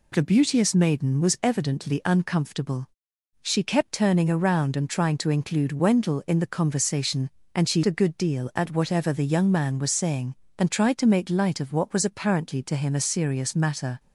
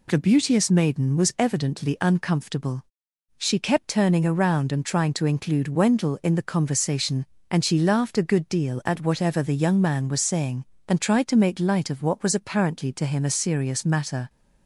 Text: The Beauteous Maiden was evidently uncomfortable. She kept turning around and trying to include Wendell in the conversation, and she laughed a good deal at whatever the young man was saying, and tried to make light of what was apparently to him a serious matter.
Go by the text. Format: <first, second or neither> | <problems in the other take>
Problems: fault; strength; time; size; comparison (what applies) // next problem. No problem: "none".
second | skips "laughed"; at 7.8 s